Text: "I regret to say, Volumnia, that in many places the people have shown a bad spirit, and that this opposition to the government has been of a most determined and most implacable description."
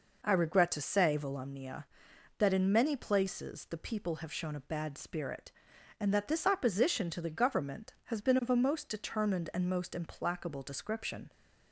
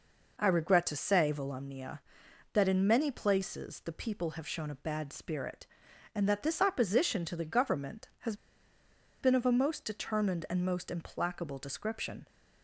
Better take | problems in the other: first | pauses between "has" and "been"; noticeable; at 8.3 s; 0.85 s long

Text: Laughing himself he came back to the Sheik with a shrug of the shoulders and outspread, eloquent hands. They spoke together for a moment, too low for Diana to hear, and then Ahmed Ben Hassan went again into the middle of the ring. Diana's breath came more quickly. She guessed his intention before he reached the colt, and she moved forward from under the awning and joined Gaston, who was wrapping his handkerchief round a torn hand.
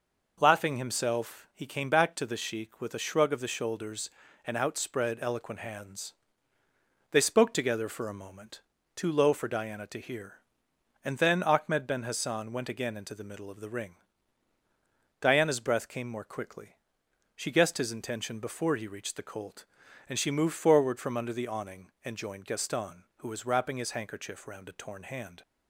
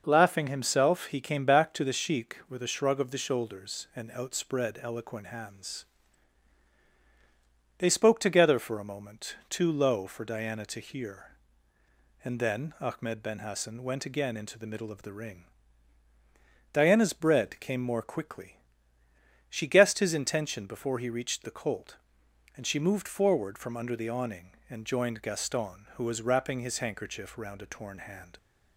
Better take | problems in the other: first | says "bread" for "breath"; at 17.1 s

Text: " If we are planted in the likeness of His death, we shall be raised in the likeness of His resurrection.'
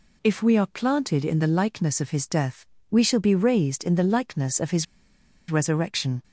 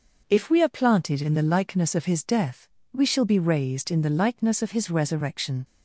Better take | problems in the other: second | pauses between "His" and "resurrection"; noticeable; at 4.8 s; 0.63 s long

